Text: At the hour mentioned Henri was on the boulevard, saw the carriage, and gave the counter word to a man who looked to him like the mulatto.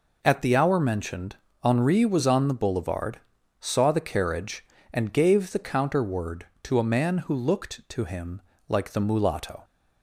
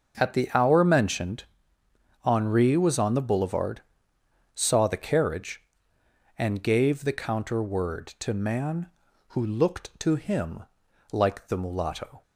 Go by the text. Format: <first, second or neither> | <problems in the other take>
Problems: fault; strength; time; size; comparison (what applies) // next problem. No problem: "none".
first | starts louder than the rest; until 1.2 s; 6 dB // pauses between "mentioned" and "Henri"; noticeable; at 1.4 s; 0.80 s long; slight in the first // skips "a"; at 8.3 s // pauses between "him" and "like"; noticeable; at 10.6 s; 0.48 s long; slight in the first